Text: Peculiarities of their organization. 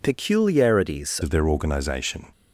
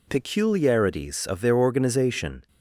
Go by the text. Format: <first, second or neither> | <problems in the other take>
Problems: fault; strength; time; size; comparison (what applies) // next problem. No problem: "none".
second | changes voice at "of"; from 1.2 s on; 1.1 s long